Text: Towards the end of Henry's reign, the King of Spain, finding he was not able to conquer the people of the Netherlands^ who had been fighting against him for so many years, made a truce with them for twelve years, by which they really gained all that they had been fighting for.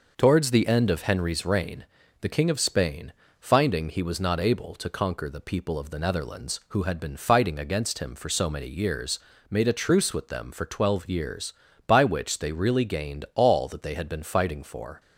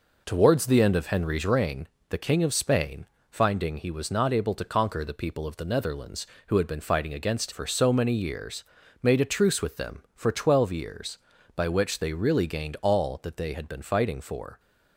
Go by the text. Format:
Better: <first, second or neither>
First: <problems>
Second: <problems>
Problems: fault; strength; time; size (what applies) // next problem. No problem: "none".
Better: first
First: none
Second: skips "him"; at 7.5 s